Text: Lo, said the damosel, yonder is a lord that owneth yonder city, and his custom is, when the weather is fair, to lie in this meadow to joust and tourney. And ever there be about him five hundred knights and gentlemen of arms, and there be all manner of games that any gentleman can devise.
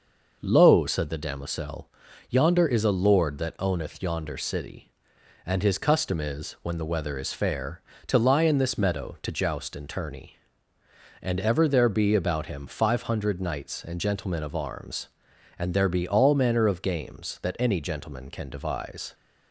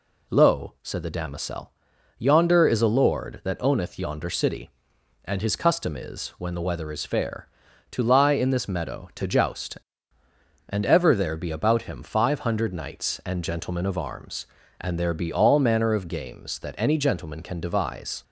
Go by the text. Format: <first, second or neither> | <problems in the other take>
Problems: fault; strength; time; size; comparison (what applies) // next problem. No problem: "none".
first | skips "and tourney"; at 10.2 s